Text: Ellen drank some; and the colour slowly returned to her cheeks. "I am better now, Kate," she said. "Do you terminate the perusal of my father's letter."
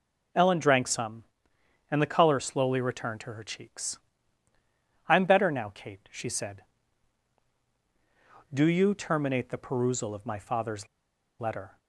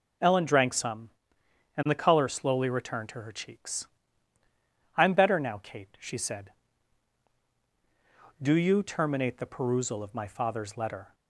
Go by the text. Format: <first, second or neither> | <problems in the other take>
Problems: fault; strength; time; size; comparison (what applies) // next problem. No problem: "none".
second | pauses between "father's" and "letter"; noticeable; at 10.8 s; 0.52 s long